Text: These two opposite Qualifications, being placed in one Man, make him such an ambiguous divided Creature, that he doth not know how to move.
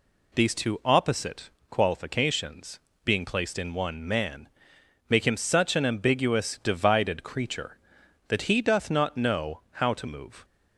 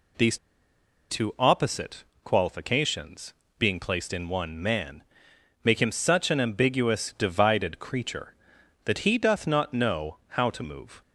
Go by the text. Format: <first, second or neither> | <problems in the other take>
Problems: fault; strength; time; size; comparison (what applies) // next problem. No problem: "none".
first | pauses between "These" and "two"; noticeable; at 0.3 s; 0.72 s long // pauses between "opposite" and "Qualifications"; slight; at 2.0 s; 0.20 s long; slight in the first